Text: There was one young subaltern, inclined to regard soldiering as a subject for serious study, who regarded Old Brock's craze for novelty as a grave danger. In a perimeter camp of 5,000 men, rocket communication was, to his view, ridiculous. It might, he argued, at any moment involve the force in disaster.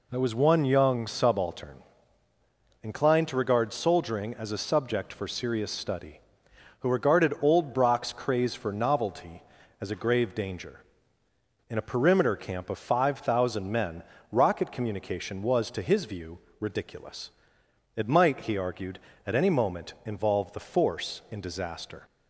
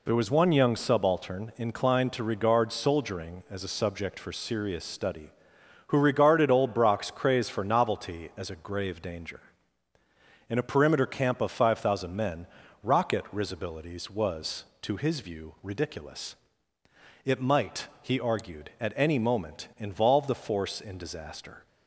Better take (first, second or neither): first